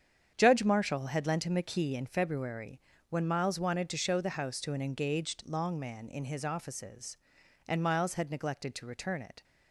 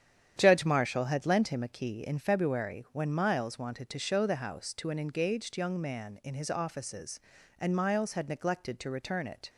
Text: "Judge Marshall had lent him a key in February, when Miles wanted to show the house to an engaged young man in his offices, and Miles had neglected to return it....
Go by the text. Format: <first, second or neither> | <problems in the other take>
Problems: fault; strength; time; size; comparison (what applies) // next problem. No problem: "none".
second | starts louder than the rest; strong; until 1.3 s; 8 dB; strong in the second // says "long" for "young"; at 5.4 s